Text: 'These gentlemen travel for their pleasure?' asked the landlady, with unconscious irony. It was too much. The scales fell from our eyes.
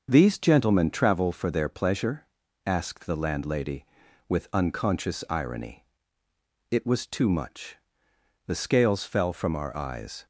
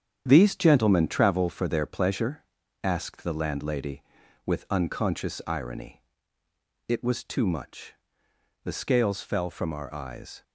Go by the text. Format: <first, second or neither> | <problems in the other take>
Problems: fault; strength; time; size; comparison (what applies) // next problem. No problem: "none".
first | gets quieter; throughout; 6.5 dB // starts louder than the rest; strong; until 1.2 s; 8.5 dB; also in the first